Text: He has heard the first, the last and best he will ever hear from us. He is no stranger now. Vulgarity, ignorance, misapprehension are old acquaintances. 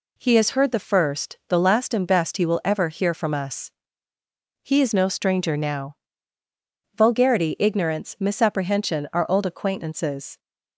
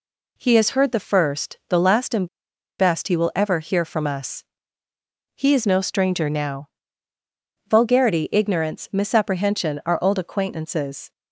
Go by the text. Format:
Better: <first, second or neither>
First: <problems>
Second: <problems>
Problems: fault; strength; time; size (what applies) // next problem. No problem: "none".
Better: first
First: none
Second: pauses between "and" and "best"; noticeable; at 2.2 s; 0.52 s long